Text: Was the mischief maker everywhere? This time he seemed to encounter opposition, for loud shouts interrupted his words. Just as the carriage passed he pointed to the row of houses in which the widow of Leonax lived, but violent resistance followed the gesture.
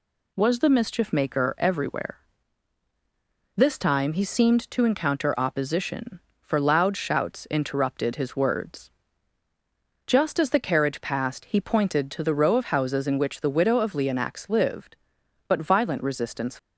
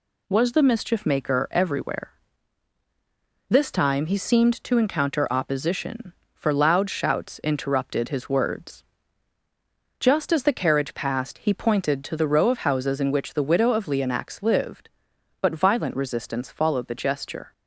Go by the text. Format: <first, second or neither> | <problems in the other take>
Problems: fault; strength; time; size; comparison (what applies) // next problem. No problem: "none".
second | stops before "followed the gesture"; at 16.5 s